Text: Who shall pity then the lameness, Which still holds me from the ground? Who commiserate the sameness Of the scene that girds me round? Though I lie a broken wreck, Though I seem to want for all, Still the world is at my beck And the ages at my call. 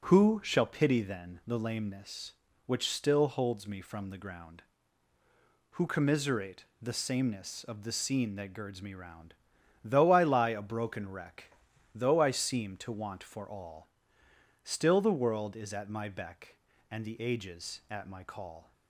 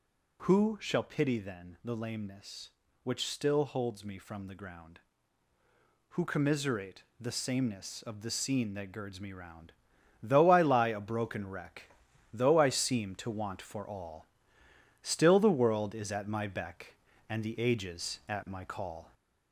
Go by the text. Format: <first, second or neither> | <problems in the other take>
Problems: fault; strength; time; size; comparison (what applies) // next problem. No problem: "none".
first | gets louder; slight; throughout; 3 dB // pauses between "commiserate" and "the"; slight; at 7.0 s; 0.16 s long; slight in the first